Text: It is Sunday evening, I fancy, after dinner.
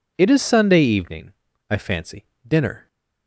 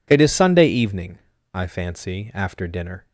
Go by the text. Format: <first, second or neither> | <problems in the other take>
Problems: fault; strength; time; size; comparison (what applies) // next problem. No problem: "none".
second | skips "after"; at 2.3 s